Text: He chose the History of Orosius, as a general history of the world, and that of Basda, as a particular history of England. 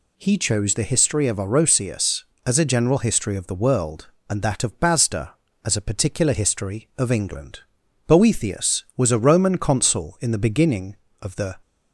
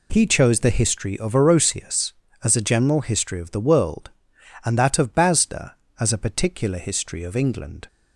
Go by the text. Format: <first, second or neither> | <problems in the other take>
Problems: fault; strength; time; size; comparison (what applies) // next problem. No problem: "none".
second | goes on to say "Boethius was a Roman Consul in the beginning of the"; strong; from 8.0 s on; 3.5 s long